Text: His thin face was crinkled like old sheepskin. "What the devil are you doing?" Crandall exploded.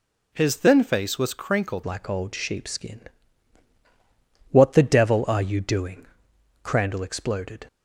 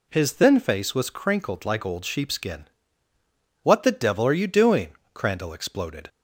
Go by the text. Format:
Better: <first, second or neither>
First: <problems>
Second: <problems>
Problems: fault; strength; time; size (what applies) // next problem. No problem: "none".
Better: second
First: changes voice at "like"; from 1.8 s on; 5.8 s long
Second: none